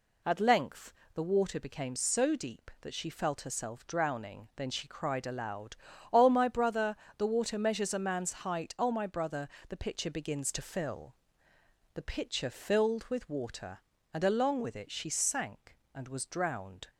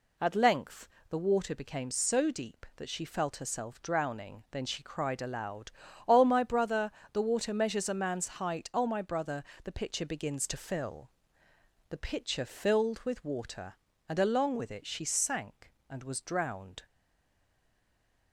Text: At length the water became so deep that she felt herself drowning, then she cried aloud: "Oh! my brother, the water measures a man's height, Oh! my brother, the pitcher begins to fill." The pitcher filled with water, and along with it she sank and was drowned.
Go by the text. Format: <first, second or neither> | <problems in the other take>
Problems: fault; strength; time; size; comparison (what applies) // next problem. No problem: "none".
first | pauses between "length" and "the"; slight; at 0.8 s; 0.22 s long; slight in the first // pauses between "man's" and "height"; slight; at 8.2 s; 0.16 s long; slight in the first // stays silent after the last word; noticeable; from 16.8 s on; 1.5 s long